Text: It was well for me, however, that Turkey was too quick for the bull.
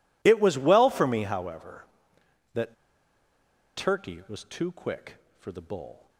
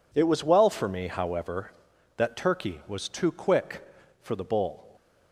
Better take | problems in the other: second | pauses between "that" and "Turkey"; at 2.7 s; 1.0 s long

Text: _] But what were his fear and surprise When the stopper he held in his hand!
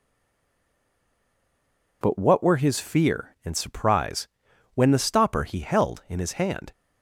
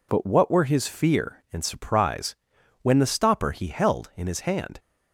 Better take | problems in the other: second | stays silent before the first word; noticeable; until 2.0 s; 2.0 s long // pauses between "surprise" and "When"; noticeable; at 4.2 s; 0.46 s long; noticeable in the second

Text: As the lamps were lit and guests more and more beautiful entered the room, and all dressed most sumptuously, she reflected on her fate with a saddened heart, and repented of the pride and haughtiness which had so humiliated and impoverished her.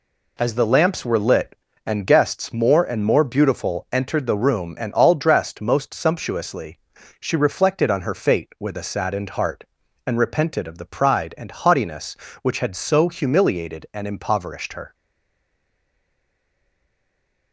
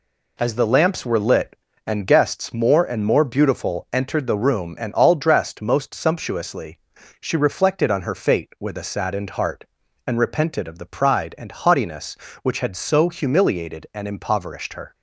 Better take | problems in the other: second | stays silent after the last word; strong; from 14.9 s on; 2.6 s long

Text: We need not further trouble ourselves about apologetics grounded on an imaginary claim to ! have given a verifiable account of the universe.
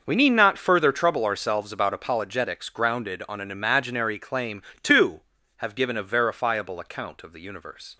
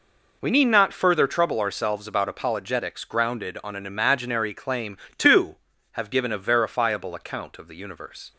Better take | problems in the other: second | gets quieter; strong; throughout; 15 dB

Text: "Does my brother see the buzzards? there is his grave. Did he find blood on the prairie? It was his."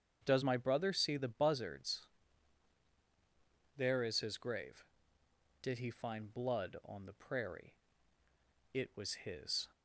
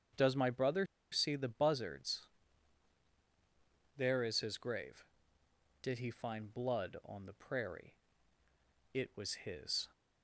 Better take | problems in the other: first | starts louder than the rest; strong; until 1.4 s; 7.5 dB; strong in the first // pauses between "brother" and "see"; slight; at 0.8 s; 0.25 s long

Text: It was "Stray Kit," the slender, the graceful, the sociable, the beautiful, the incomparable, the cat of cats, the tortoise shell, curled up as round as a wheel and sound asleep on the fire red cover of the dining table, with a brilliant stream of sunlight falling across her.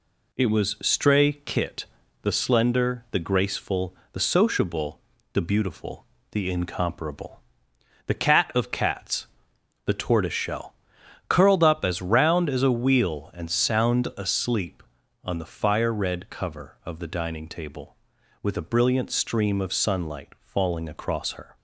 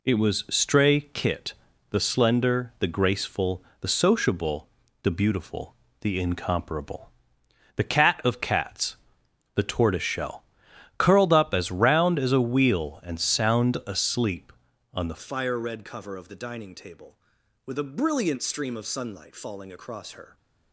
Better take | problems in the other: first | changes voice at "fire"; from 15.1 s on; 5.2 s long

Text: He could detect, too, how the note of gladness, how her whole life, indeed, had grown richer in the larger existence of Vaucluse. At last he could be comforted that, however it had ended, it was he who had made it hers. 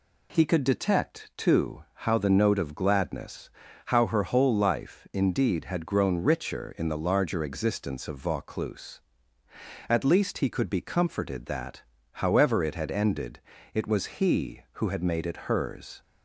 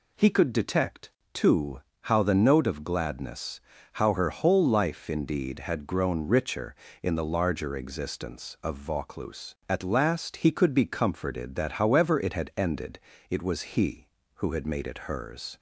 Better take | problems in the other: second | says "least" for "last"; at 10.0 s // pauses between "it" and "hers"; slight; at 15.3 s; 0.16 s long

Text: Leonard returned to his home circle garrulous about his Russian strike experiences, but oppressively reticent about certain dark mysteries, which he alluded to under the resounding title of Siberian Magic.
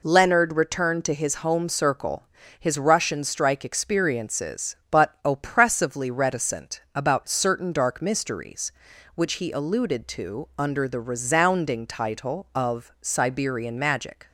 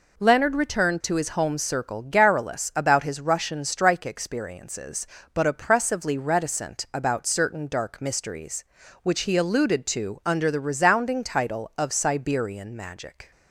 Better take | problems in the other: second | skips "garrulous about"; at 2.4 s

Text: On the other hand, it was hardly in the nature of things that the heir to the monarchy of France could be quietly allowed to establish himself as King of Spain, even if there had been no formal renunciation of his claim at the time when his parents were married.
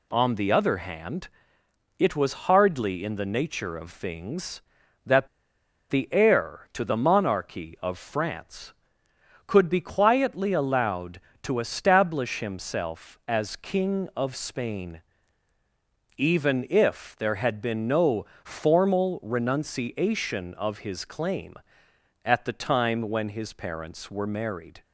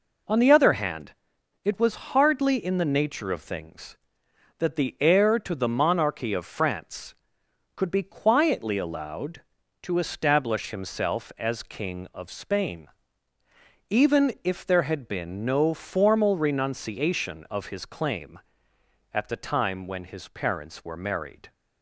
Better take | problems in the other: second | pauses between "that" and "the"; noticeable; at 5.2 s; 0.62 s long // pauses between "no" and "formal"; slight; at 18.2 s; 0.18 s long

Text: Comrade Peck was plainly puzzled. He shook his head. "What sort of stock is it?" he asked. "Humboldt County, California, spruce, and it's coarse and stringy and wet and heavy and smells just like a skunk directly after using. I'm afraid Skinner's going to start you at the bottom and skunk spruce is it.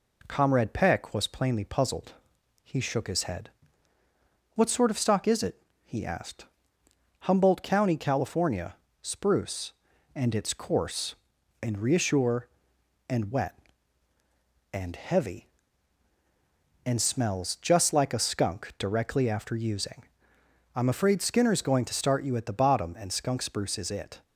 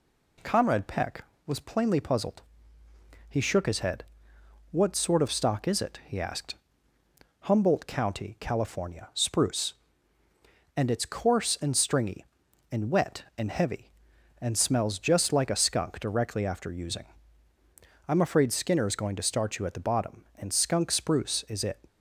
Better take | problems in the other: second | says "reassure" for "stringy"; at 11.7 s

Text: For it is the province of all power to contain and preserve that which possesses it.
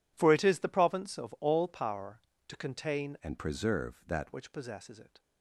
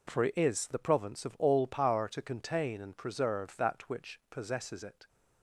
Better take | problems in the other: second | changes voice from "and" to "that"; from 3.2 to 4.3 s; 1.1 s long

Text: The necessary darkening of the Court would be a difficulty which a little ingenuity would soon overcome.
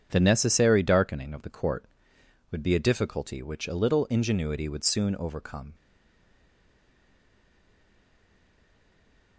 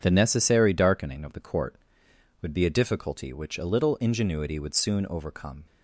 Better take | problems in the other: second | stays silent after the last word; strong; from 5.7 s on; 3.6 s long

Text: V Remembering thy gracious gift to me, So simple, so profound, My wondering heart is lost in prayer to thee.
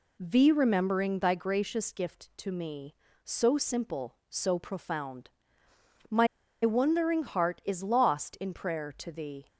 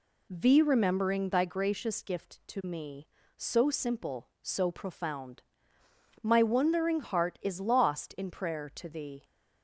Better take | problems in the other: second | pauses between "My" and "wondering"; slight; at 6.2 s; 0.35 s long

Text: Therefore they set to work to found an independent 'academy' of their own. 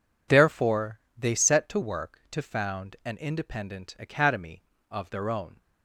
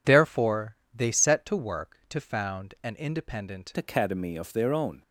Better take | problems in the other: first | pauses between "Therefore" and "they"; slight; at 0.7 s; 0.16 s long; slight in the first // changes voice at "academy"; from 3.7 s on; 1.3 s long

